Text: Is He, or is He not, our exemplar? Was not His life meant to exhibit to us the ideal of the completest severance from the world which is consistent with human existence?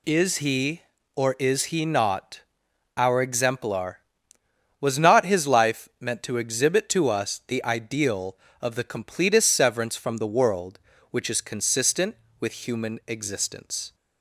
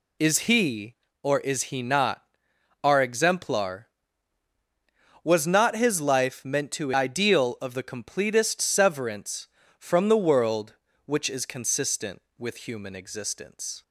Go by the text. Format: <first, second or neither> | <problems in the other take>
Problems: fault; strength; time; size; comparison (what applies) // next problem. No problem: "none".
first | skips "exhibit to us the"; at 6.9 s